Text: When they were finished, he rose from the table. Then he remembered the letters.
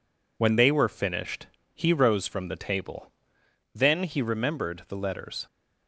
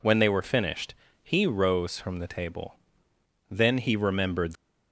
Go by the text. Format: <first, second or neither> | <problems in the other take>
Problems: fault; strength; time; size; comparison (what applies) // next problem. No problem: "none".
first | stops before "the letters"; at 4.5 s